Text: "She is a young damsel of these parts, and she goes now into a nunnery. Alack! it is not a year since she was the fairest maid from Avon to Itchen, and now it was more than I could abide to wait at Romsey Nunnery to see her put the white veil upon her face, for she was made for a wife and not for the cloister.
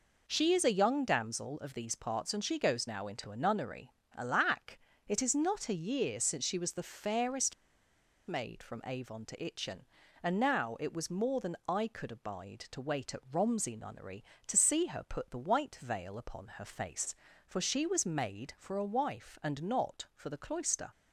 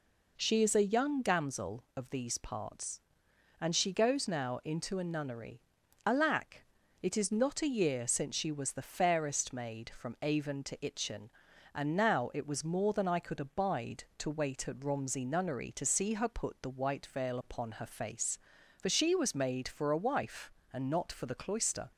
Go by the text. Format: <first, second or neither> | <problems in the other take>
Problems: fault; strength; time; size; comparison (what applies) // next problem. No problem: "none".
second | pauses between "fairest" and "maid"; noticeable; at 7.5 s; 0.72 s long